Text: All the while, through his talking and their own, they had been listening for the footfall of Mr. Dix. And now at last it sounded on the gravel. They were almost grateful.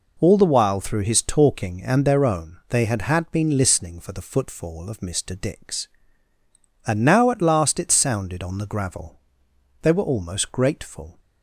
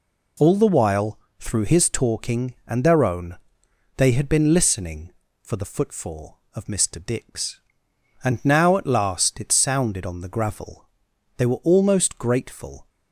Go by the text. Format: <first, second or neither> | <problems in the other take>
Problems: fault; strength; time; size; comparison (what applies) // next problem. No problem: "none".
second | says "had" twice; at 3.0 s